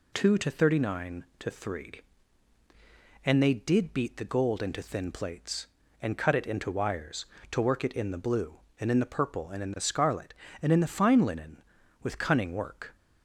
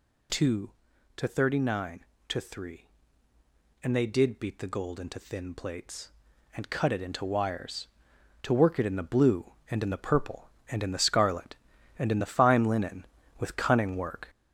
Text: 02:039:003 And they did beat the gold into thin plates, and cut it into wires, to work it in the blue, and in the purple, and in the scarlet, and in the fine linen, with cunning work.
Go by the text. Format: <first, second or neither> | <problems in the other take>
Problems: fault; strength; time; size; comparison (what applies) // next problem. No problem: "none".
first | gets louder; noticeable; throughout; 5 dB